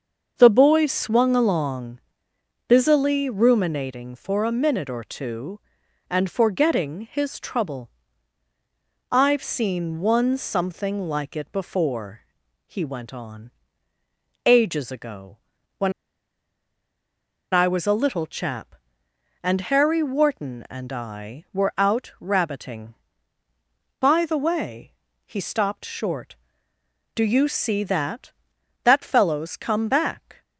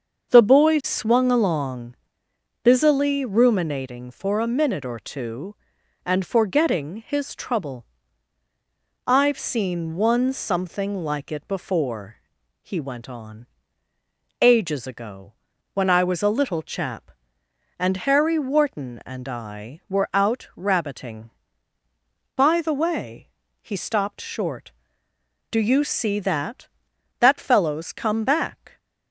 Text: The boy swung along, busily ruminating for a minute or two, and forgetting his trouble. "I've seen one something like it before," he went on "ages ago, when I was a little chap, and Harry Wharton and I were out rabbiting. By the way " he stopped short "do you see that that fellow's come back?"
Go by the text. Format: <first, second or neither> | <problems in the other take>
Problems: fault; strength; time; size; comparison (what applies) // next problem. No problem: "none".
second | starts louder than the rest; until 1.3 s; 6.5 dB; also in the second // pauses between "on" and "ages"; noticeable; at 13.5 s; 0.92 s long; noticeable in the second // pauses between "when" and "I"; strong; at 15.9 s; 1.6 s long